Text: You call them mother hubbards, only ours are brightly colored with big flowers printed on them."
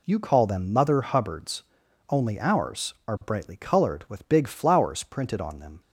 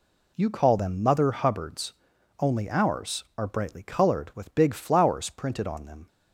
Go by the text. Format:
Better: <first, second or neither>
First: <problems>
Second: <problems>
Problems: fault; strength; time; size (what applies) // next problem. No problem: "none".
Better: neither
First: none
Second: none